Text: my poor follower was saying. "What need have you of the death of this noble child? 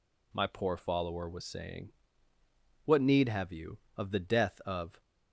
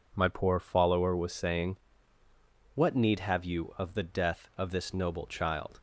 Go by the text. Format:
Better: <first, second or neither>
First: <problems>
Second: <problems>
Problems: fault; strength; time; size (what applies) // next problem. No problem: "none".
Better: second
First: stops before "this noble child"; at 5.0 s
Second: none